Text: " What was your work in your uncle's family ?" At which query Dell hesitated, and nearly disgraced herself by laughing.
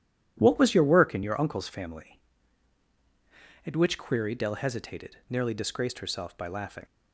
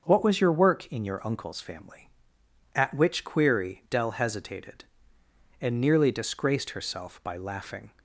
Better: second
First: starts louder than the rest; strong; until 1.3 s; 10.5 dB // skips "and"; at 5.2 s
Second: none

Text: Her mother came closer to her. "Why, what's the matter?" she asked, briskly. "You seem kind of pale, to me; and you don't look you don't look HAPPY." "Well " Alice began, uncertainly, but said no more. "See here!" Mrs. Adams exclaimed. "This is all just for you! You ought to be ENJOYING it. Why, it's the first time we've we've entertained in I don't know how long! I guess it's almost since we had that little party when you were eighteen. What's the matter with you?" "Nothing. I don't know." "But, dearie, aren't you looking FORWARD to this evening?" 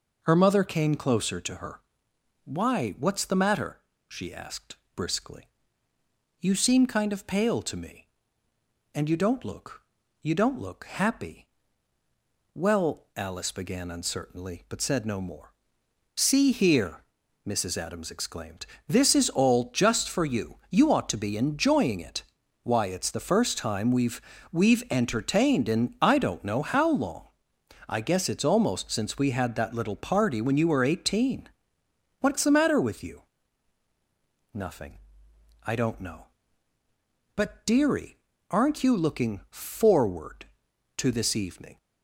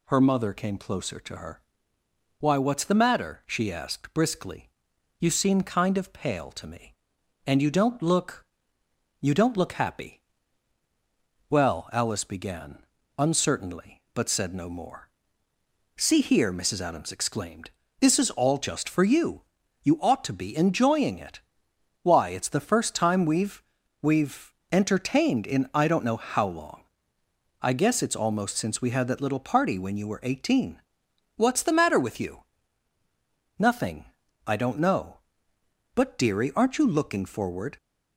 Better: first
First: pauses between "look" and "you"; at 9.8 s; 0.44 s long // pauses between "we've" and "we've"; slight; at 24.2 s; 0.32 s long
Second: pauses between "look" and "you"; noticeable; at 8.4 s; 0.76 s long // pauses between "we've" and "we've"; at 23.6 s; 0.38 s long // pauses between "we've" and "entertained"; slight; at 24.5 s; 0.20 s long // stops before "to this evening"; at 37.7 s

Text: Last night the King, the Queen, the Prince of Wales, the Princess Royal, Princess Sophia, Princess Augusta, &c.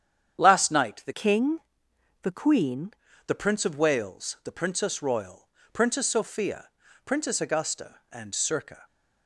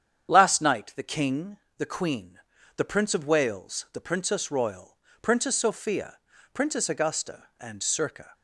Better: second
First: starts louder than the rest; strong; until 1.4 s; 8.5 dB // changes voice from "King" to "Queen"; from 1.1 to 2.9 s; 1.8 s long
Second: starts louder than the rest; strong; until 1.3 s; 8.5 dB

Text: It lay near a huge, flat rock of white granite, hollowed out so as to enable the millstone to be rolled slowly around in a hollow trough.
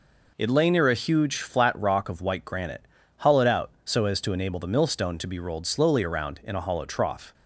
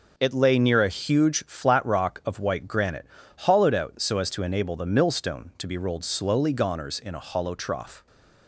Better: first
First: none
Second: says "goners" for "around"; at 6.5 s

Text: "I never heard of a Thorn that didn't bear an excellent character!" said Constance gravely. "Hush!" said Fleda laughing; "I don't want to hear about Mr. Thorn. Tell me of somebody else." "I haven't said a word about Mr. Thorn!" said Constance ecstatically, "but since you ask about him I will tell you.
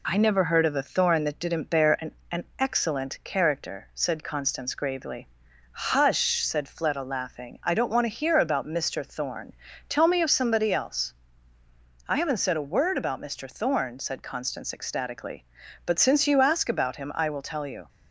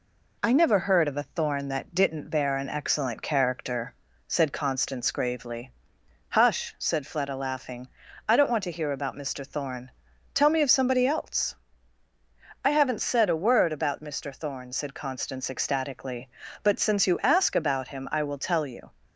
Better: second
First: says "an" twice; at 2.2 s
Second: none

